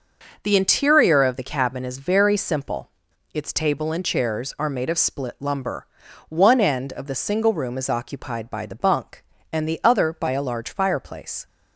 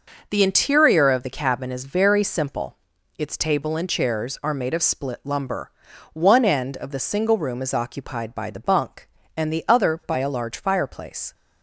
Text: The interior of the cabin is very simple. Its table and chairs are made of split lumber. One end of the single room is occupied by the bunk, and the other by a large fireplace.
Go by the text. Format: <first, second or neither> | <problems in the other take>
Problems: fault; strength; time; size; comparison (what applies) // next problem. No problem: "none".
neither | none